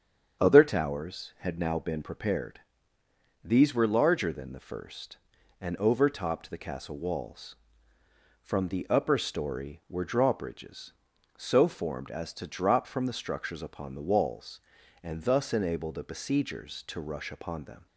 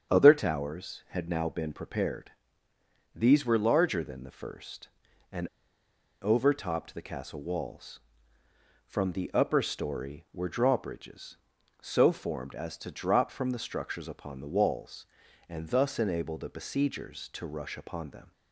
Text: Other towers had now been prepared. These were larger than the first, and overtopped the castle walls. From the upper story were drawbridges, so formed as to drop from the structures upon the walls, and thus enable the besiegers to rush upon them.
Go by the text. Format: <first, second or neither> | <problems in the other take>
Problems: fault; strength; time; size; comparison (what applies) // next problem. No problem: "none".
first | starts louder than the rest; strong; until 1.1 s; 7.5 dB; strong in the first // pauses between "and" and "overtopped"; noticeable; at 5.4 s; 0.75 s long